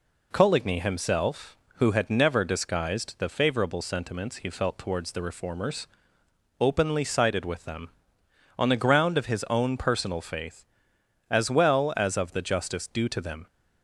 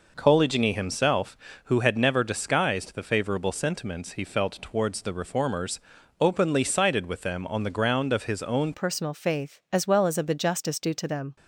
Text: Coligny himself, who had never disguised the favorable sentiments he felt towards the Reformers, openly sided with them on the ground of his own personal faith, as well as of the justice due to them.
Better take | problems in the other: first | changes voice at "personal"; from 8.7 s on; 2.6 s long

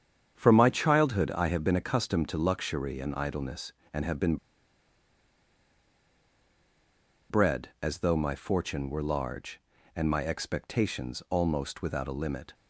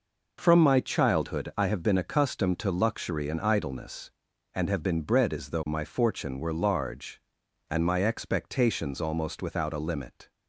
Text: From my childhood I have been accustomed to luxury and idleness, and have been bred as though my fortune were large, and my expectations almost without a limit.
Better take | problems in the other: second | starts louder than the rest; strong; until 1.4 s; 8 dB // pauses between "been" and "bred"; strong; at 4.3 s; 2.9 s long

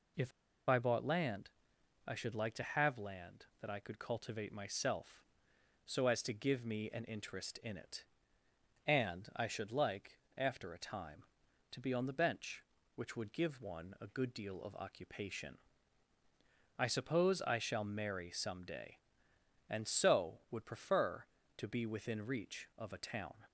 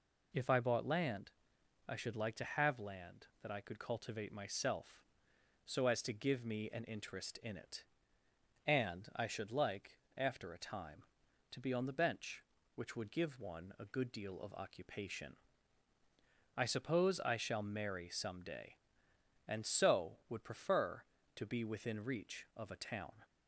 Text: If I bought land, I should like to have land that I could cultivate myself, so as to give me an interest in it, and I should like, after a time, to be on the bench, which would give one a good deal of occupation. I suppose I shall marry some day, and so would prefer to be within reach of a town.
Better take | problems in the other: second | pauses between "If" and "I"; at 0.3 s; 0.37 s long

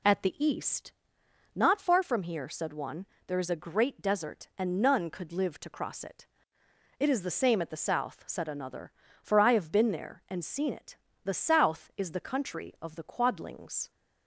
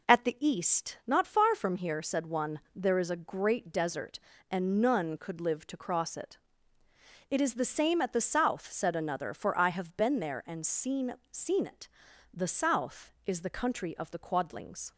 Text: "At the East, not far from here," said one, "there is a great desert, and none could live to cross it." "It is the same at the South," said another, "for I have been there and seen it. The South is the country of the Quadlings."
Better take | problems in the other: first | says "seen" twice; at 11.3 s

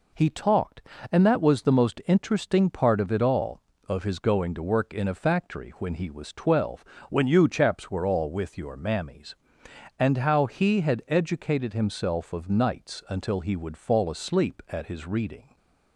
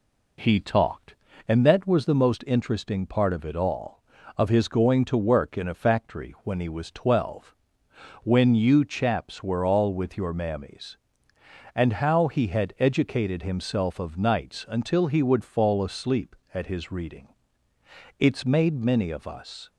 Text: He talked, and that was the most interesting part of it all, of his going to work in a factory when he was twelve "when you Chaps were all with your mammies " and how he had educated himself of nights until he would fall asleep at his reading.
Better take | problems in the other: first | pauses between "twelve" and "when"; noticeable; at 7.5 s; 0.70 s long; slight in the first // goes on to say "It's made many of us"; from 18.1 s on; 1.5 s long

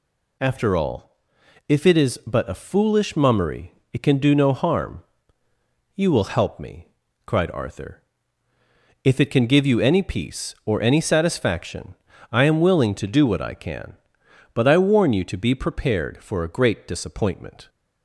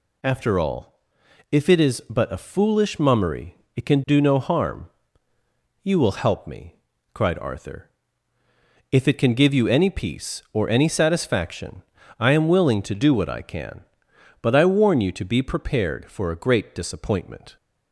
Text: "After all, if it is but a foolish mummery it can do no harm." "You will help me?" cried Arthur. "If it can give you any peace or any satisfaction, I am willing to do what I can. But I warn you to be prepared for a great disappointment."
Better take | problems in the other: neither | pauses between "mummery" and "it"; slight; the same in both

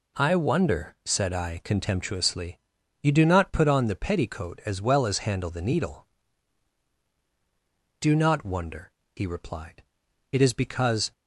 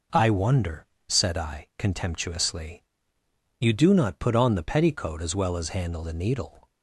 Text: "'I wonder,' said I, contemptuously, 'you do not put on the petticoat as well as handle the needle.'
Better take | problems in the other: second | goes on to say "Do not wonder he replied it is because"; strong; from 7.9 s on; 3.1 s long

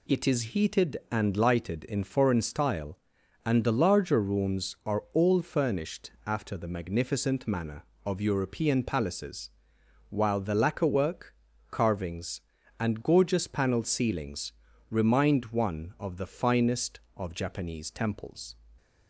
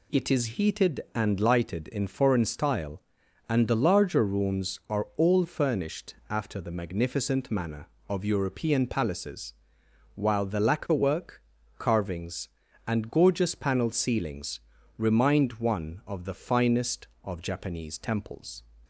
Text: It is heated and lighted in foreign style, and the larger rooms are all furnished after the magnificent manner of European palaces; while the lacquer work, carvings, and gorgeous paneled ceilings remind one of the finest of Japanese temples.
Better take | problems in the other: neither | pauses between "ceilings" and "remind"; the same in both

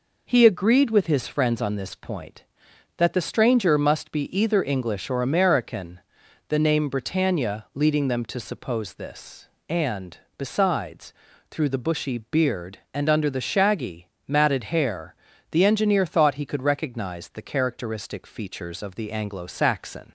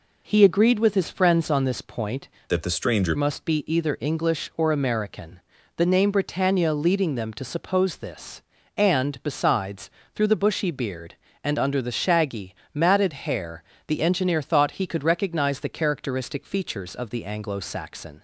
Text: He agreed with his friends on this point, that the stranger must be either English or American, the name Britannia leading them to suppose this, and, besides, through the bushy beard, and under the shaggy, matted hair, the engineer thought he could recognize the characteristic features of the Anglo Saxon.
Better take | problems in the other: first | changes voice from "that" to "stranger"; from 2.4 to 3.1 s; 0.7 s long

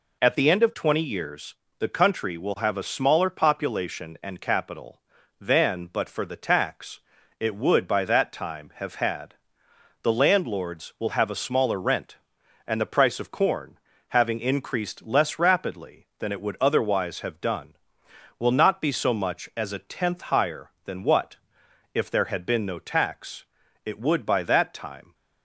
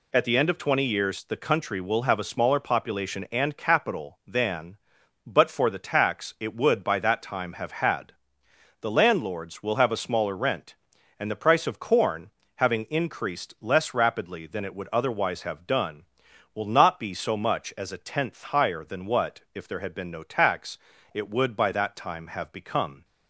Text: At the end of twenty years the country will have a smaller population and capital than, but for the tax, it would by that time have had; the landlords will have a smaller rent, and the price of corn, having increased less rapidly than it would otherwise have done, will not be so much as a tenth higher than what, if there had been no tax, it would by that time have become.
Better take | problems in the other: second | pauses between "years" and "the"; slight; at 1.5 s; 0.24 s long // stops before "have become"; at 25.1 s

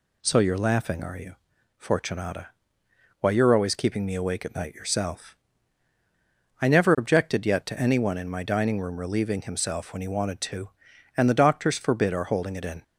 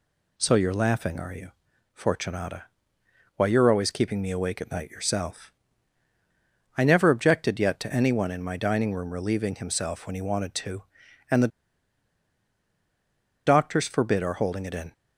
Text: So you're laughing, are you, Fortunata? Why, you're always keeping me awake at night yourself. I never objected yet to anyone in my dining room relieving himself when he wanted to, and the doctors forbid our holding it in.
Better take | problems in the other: first | pauses between "the" and "doctors"; strong; at 11.4 s; 1.9 s long

